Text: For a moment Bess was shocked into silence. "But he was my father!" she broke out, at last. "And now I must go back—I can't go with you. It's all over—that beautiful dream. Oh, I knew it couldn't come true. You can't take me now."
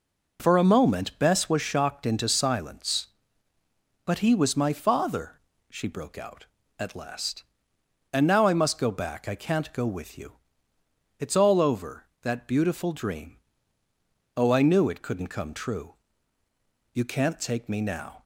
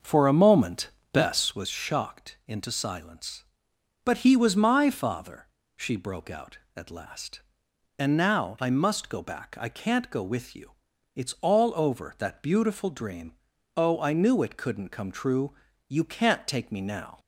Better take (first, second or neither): first